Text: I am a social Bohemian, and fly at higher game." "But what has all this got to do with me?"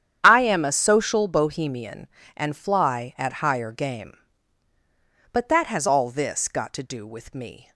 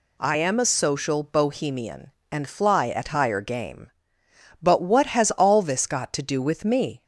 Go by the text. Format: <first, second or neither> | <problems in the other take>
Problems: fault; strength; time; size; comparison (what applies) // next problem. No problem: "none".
second | starts louder than the rest; strong; until 1.2 s; 9.5 dB // says "that" for "what"; at 5.4 s